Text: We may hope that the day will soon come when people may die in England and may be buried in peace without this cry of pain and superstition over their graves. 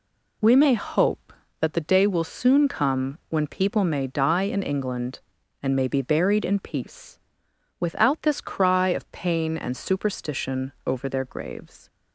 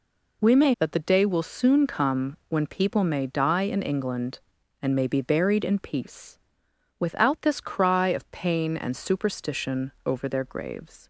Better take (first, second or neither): first